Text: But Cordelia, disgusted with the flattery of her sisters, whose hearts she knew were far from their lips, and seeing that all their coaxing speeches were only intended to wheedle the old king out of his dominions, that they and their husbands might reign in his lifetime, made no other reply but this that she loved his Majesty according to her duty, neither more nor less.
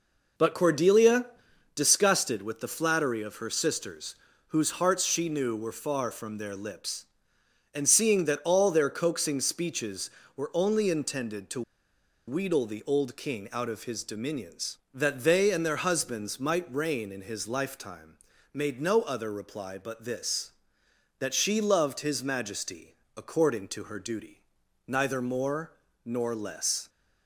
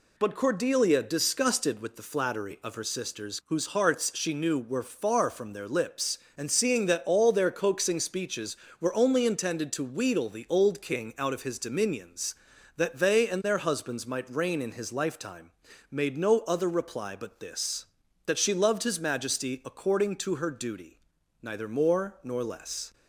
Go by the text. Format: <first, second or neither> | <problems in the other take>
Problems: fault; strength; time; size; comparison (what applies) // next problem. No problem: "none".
second | pauses between "to" and "wheedle"; noticeable; at 11.6 s; 0.66 s long // pauses between "Majesty" and "according"; slight; at 22.9 s; 0.20 s long // pauses between "more" and "nor"; slight; at 25.7 s; 0.30 s long